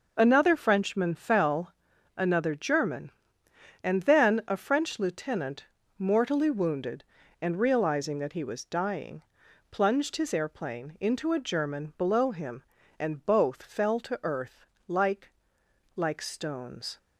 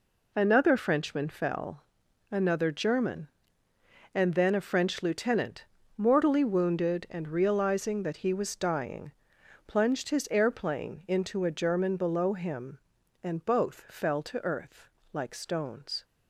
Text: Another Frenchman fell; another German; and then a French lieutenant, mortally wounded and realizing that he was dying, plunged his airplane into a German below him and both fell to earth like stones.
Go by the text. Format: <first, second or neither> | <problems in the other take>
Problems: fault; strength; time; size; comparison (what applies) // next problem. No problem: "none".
second | pauses between "earth" and "like"; slight; at 14.6 s; 0.22 s long; slight in the second // says "like" twice; at 15.9 s